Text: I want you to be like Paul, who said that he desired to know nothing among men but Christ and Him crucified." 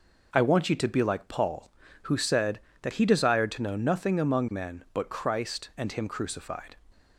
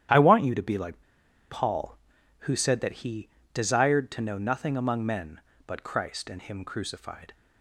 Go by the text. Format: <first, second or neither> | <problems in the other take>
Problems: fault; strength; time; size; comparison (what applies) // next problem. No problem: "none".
first | starts louder than the rest; strong; until 1.6 s; 10.5 dB // pauses between "like" and "Paul"; noticeable; at 1.0 s; 0.49 s long // pauses between "he" and "desired"; slight; at 3.2 s; 0.26 s long